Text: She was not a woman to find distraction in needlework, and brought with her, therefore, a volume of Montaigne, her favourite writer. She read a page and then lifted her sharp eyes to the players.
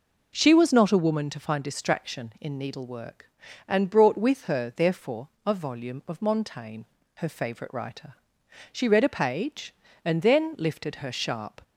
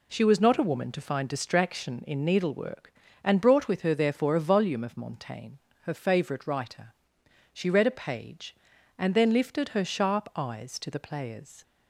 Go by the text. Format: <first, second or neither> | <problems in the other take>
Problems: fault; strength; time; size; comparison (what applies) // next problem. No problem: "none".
second | stops before "eyes to the players"; at 11.6 s